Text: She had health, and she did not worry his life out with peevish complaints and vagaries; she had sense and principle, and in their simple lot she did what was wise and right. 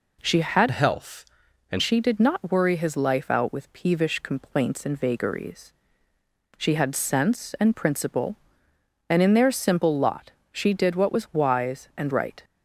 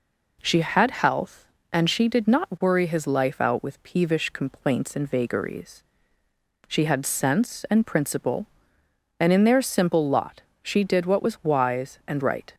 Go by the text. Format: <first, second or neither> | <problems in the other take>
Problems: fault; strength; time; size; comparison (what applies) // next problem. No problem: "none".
second | changes voice from "health" to "and"; from 0.6 to 1.8 s; 1.2 s long // pauses between "lot" and "she"; slight; at 10.3 s; 0.22 s long; slight in the second